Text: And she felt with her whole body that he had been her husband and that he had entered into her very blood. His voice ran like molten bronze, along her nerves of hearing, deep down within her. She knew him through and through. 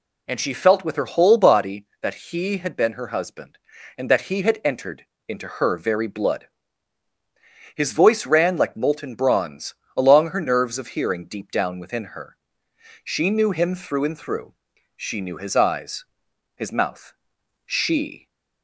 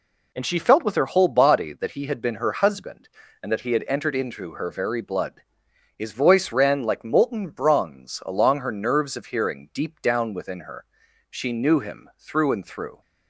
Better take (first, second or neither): second